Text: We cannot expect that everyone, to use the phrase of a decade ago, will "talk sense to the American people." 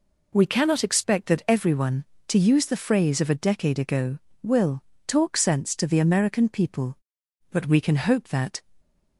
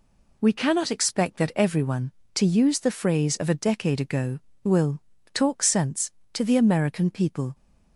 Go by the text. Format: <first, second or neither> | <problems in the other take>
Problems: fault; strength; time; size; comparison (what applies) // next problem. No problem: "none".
second | pauses between "will" and "talk"; slight; at 4.8 s; 0.24 s long; slight in the second // goes on to say "But we can hope that"; noticeable; from 7.5 s on; 1.1 s long